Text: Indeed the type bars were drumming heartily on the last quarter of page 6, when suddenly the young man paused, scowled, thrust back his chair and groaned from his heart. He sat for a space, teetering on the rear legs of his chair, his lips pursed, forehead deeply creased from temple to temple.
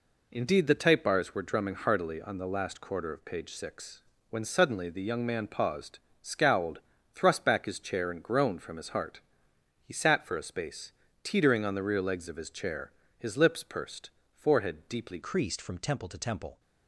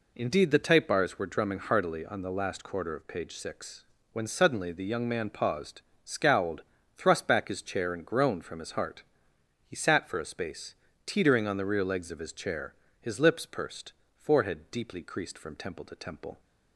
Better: second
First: changes voice at "creased"; from 15.2 s on; 1.3 s long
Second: none

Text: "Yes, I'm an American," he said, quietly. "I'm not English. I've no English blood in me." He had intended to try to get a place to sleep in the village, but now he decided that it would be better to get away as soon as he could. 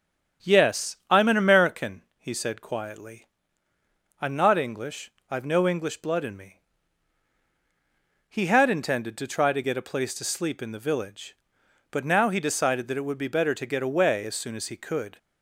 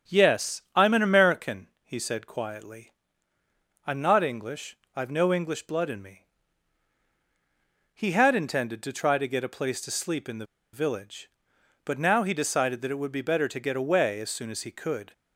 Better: first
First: starts louder than the rest; strong; until 1.5 s; 8 dB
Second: starts louder than the rest; strong; until 1.2 s; 8 dB // pauses between "the" and "village"; slight; at 10.4 s; 0.27 s long

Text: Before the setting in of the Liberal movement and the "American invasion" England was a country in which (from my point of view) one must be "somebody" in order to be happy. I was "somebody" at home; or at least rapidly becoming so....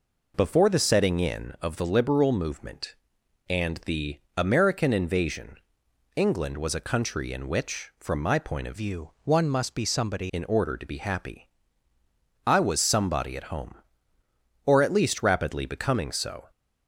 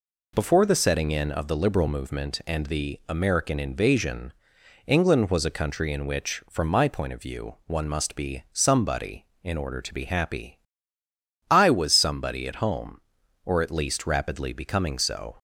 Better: second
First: pauses between "the" and "American"; slight; at 4.1 s; 0.16 s long // pauses between "invasion" and "England"; noticeable; at 5.5 s; 0.62 s long // changes voice from "view" to "somebody"; from 8.7 to 10.2 s; 1.5 s long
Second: pauses between "invasion" and "England"; noticeable; at 4.3 s; 0.56 s long

